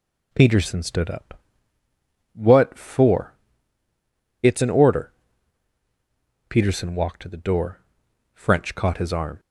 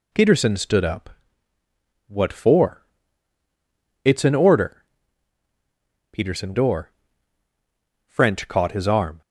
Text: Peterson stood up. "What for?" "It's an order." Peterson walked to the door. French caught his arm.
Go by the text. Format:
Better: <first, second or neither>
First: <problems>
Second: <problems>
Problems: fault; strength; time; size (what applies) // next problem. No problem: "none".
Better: first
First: none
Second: skips "walked to the"; at 6.5 s